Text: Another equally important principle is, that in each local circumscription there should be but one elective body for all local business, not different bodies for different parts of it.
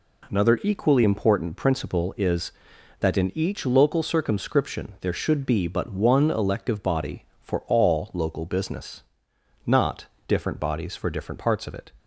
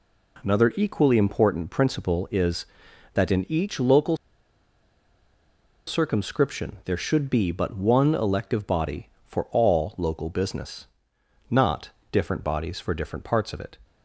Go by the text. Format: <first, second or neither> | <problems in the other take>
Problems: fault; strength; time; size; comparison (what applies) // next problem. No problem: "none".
first | pauses between "local" and "circumscription"; strong; at 4.1 s; 1.7 s long // pauses between "not" and "different"; slight; at 11.8 s; 0.24 s long; slight in the first